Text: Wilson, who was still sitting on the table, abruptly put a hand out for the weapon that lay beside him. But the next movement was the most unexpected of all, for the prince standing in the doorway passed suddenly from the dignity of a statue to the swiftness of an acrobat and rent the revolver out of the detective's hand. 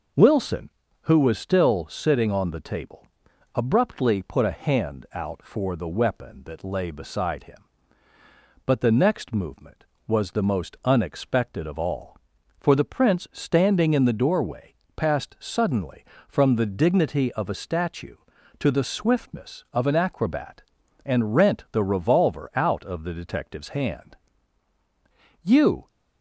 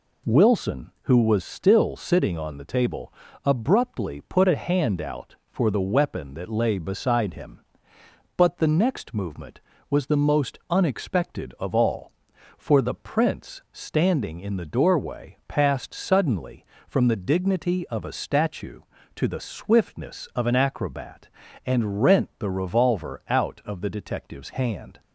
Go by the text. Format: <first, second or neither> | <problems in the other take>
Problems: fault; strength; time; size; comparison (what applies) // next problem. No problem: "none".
second | pauses between "doorway" and "passed"; slight; at 14.7 s; 0.24 s long // goes on to say "You"; slight; from 25.4 s on; 0.46 s long